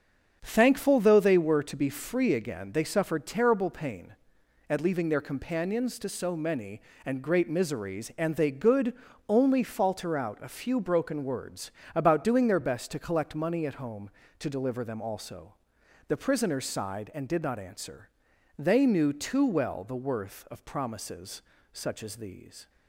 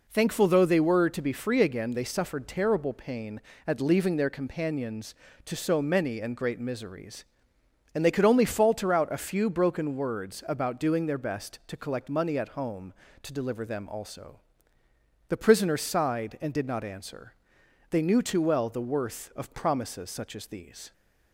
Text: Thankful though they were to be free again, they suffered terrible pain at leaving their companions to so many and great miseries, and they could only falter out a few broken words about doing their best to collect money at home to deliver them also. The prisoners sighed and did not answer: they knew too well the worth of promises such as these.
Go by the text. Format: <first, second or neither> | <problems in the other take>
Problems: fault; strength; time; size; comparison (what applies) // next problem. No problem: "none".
second | starts louder than the rest; until 1.4 s; 7 dB // says "good" for "could"; at 8.5 s // pauses between "words" and "about"; slight; at 11.7 s; 0.24 s long // pauses between "promises" and "such"; slight; at 21.4 s; 0.32 s long